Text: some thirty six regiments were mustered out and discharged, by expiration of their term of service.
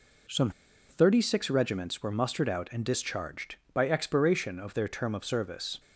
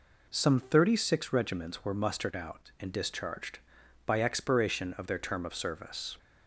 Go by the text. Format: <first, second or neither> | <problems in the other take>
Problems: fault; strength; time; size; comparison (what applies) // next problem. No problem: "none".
second | pauses between "some" and "thirty"; at 0.4 s; 0.39 s long